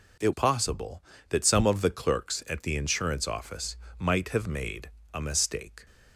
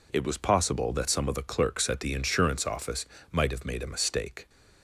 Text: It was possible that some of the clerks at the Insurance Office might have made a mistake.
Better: second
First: skips "was"; at 0.3 s // pauses between "Office" and "might"; slight; at 3.7 s; 0.24 s long // pauses between "made" and "a"; slight; at 4.8 s; 0.24 s long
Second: pauses between "Office" and "might"; slight; at 3.0 s; 0.26 s long

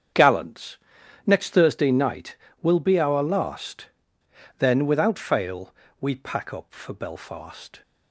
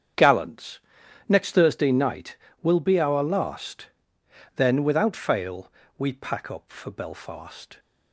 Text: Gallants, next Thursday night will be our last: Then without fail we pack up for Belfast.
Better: neither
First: starts louder than the rest; strong; until 1.6 s; 8 dB // pauses between "fail" and "we"; slight; at 5.7 s; 0.26 s long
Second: starts louder than the rest; strong; until 1.6 s; 8 dB // pauses between "fail" and "we"; slight; at 5.7 s; 0.26 s long

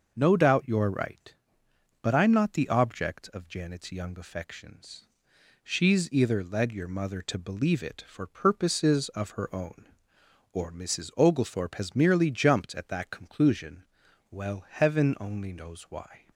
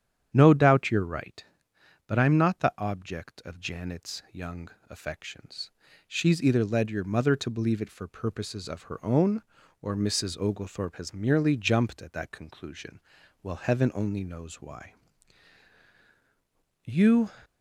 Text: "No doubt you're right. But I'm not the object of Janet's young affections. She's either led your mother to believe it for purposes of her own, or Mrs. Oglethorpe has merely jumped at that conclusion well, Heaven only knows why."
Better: first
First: starts louder than the rest; noticeable; until 1.1 s; 6 dB // pauses between "conclusion" and "well"; at 13.8 s; 0.44 s long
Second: starts louder than the rest; strong; until 1.3 s; 9 dB // pauses between "young" and "affections"; slight; at 4.6 s; 0.22 s long // pauses between "conclusion" and "well"; at 12.9 s; 0.42 s long // goes on to say "You"; slight; from 16.8 s on; 0.46 s long

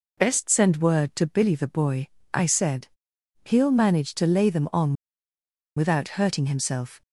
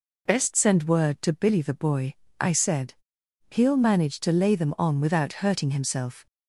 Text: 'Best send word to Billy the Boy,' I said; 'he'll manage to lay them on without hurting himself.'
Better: second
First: pauses between "on" and "without"; noticeable; at 4.9 s; 0.84 s long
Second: none

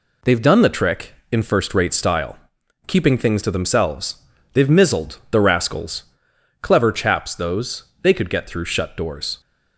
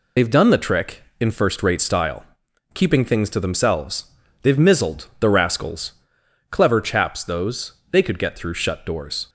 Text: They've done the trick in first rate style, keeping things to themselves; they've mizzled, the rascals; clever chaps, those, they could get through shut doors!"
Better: first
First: none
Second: loses the start of "They've"; at 0.1 s; 50 ms

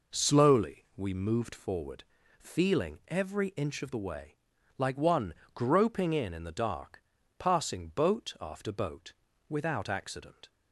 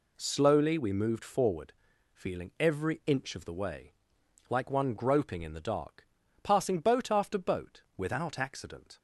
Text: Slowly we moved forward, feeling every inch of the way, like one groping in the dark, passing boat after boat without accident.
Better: second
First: pauses between "one" and "groping"; slight; at 5.3 s; 0.22 s long // says "in" twice; at 6.3 s // pauses between "boat" and "without"; slight; at 9.1 s; 0.36 s long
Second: none

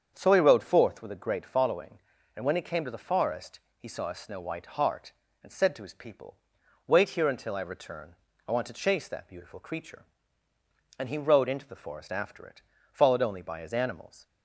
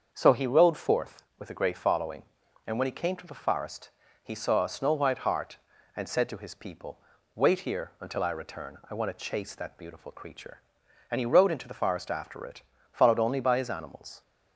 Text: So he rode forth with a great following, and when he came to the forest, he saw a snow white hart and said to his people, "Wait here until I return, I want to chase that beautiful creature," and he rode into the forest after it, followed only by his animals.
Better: neither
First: starts louder than the rest; strong; until 1.1 s; 7.5 dB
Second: starts louder than the rest; until 1.1 s; 7 dB

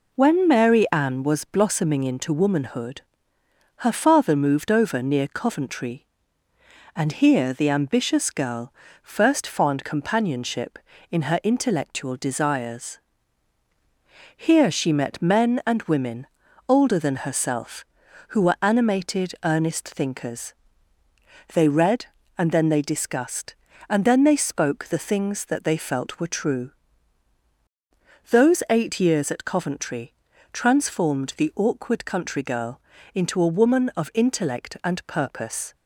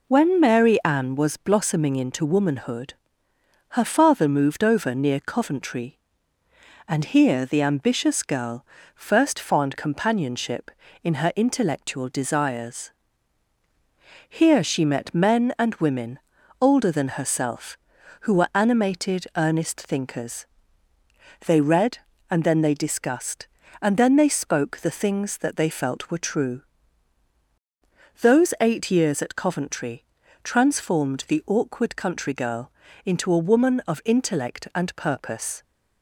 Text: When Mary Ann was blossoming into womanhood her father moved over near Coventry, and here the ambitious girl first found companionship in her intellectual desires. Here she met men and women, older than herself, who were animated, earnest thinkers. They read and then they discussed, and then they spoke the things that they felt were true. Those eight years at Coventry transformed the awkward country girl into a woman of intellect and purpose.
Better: neither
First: pauses between "womanhood" and "her"; noticeable; at 2.9 s; 0.76 s long // pauses between "girl" and "first"; slight; at 8.7 s; 0.28 s long // pauses between "Coventry" and "transformed"; at 30.1 s; 0.40 s long // pauses between "girl" and "into"; slight; at 32.7 s; 0.34 s long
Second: pauses between "womanhood" and "her"; noticeable; at 2.9 s; 0.76 s long // pauses between "girl" and "first"; slight; at 8.6 s; 0.28 s long // pauses between "Coventry" and "transformed"; at 30.0 s; 0.40 s long // pauses between "girl" and "into"; slight; at 32.7 s; 0.34 s long

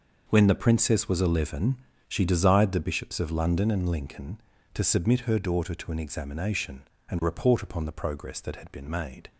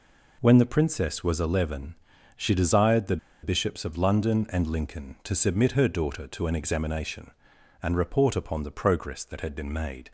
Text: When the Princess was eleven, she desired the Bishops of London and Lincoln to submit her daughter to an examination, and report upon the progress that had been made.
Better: first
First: none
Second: pauses between "the" and "Bishops"; slight; at 3.1 s; 0.25 s long

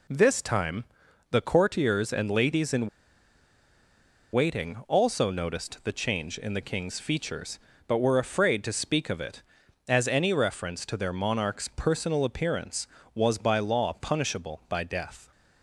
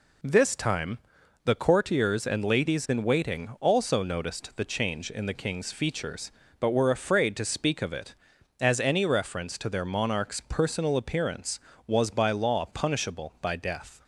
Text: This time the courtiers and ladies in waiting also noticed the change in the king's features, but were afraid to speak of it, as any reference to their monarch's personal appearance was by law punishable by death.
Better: second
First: pauses between "time" and "the"; noticeable; at 0.8 s; 0.46 s long // pauses between "in" and "waiting"; strong; at 2.8 s; 1.4 s long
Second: pauses between "time" and "the"; noticeable; at 0.9 s; 0.46 s long

